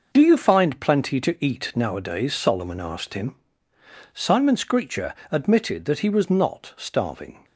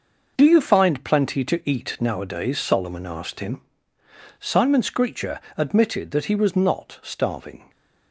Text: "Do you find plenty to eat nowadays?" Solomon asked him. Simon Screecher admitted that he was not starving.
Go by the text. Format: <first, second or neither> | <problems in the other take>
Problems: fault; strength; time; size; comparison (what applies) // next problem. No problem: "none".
neither | pauses between "Screecher" and "admitted"; slight; the same in both